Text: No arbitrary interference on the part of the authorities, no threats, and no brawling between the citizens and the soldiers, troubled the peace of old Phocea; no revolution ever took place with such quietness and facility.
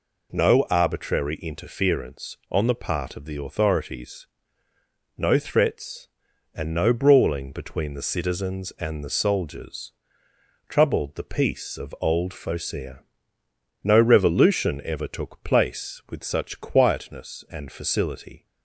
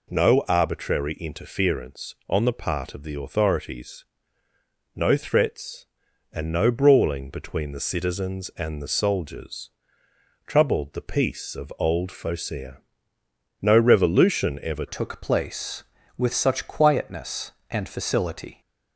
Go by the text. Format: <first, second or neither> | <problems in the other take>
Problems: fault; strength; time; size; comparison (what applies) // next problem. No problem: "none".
first | changes voice at "took"; from 14.8 s on; 3.8 s long